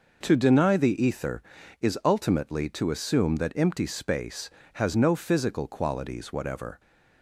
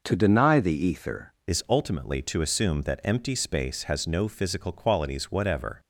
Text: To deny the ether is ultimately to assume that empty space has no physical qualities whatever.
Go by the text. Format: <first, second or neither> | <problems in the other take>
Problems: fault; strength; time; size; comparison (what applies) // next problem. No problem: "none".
first | changes voice at "is"; from 1.4 s on; 4.3 s long